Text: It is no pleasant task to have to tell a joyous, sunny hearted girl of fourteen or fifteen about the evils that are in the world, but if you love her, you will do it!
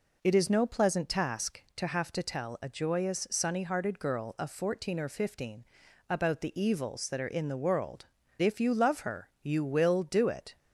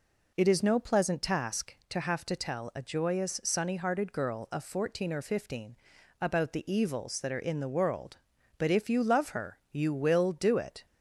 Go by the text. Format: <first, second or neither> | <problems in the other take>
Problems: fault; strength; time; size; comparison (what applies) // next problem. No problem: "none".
second | pauses between "fifteen" and "about"; noticeable; at 5.6 s; 0.46 s long; noticeable in the second // skips "but"; at 8.2 s